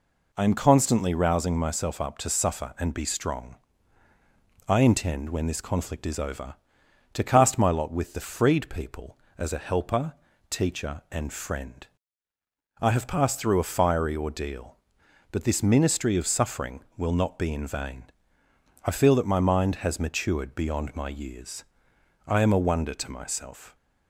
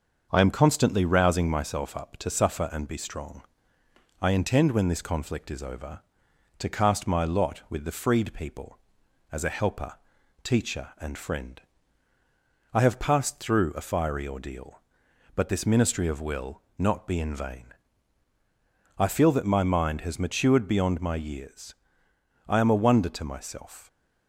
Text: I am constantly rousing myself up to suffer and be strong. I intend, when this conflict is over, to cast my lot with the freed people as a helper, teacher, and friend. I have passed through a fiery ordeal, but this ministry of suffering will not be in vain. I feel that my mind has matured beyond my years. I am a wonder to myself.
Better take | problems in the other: first | starts louder than the rest; until 1.3 s; 6.5 dB // skips "suffering"; at 16.2 s // pauses between "will" and "not"; slight; at 16.6 s; 0.16 s long

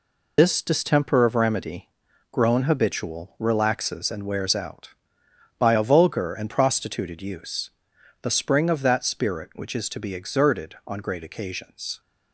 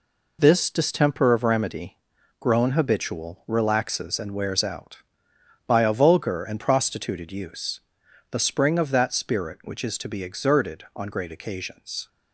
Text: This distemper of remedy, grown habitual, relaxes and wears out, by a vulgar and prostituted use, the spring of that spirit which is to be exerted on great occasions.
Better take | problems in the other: second | loses the start of "This"; at 0.3 s; 75 ms

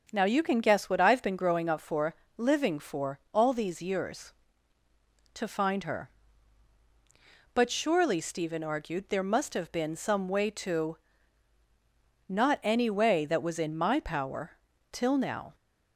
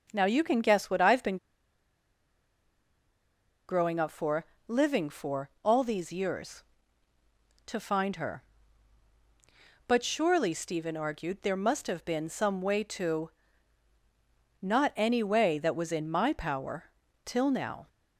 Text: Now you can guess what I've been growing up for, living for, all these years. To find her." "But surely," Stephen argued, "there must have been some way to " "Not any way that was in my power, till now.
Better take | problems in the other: first | starts louder than the rest; until 1.1 s; 7 dB; also in the first // pauses between "been" and "growing"; strong; at 1.3 s; 2.3 s long

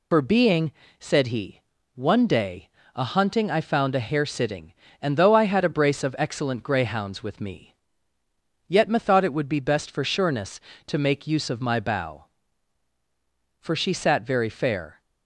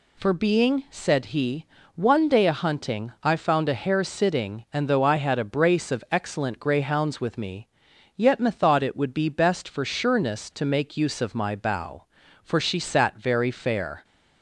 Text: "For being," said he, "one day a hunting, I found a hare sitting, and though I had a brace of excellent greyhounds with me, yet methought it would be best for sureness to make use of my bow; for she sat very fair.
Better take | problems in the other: second | loses the start of "For"; at 0.1 s; 65 ms // pauses between "day" and "a"; slight; at 2.6 s; 0.26 s long

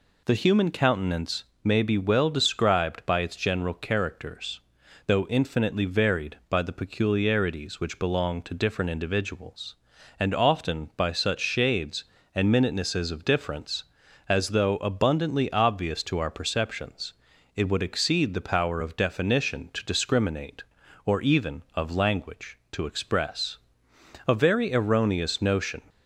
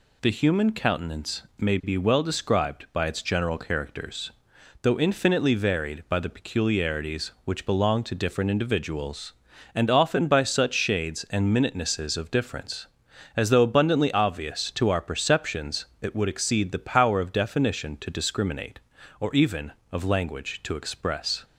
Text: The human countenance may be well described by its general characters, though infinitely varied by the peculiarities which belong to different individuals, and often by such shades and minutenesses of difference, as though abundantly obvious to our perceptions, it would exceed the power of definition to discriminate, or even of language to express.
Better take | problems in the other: second | pauses between "countenance" and "may"; slight; at 1.4 s; 0.22 s long // goes on to say "A very erroneous notion"; from 24.2 s on; 1.5 s long

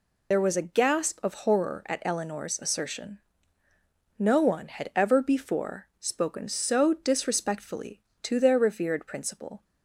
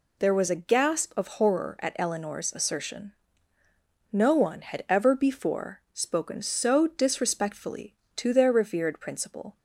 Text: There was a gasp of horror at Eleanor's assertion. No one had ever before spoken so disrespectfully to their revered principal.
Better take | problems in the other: second | loses the start of "There"; at 0.3 s; 50 ms

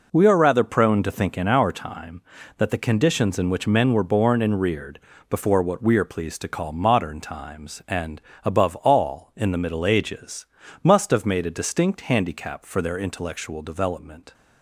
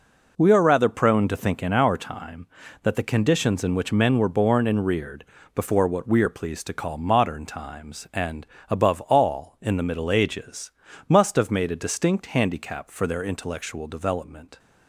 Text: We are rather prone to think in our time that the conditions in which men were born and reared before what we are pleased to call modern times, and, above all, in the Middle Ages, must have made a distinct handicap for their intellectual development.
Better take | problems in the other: neither | pauses between "reared" and "before"; slight; the same in both

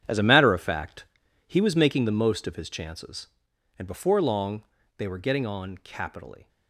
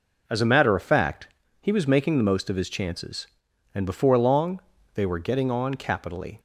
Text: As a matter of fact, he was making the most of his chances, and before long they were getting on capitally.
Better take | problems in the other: second | gets quieter; strong; throughout; 13 dB // pauses between "long" and "they"; slight; at 4.6 s; 0.34 s long; slight in the second

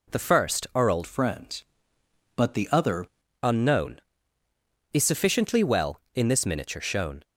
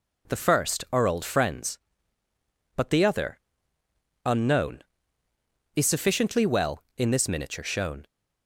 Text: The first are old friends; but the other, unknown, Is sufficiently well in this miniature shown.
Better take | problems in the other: second | changes voice from "friends" to "other"; from 1.0 to 3.0 s; 2.0 s long

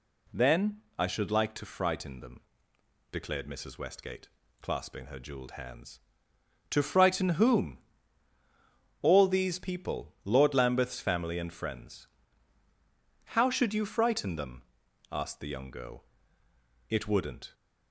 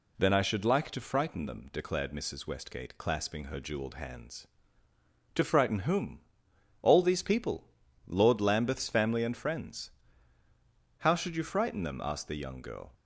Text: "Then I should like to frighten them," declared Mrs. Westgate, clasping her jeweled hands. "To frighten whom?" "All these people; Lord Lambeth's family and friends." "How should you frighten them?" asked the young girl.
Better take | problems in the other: second | pauses between "Then" and "I"; slight; at 0.8 s; 0.16 s long // goes on to say "It wouldn't"; noticeable; from 16.8 s on; 0.64 s long

